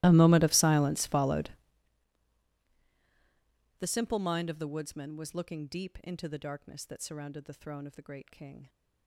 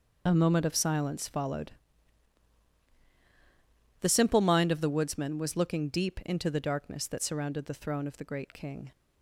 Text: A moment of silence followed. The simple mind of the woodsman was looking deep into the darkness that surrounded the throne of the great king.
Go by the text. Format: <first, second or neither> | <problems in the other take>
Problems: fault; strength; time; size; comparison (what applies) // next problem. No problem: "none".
second | starts louder than the rest; strong; until 1.8 s; 17.5 dB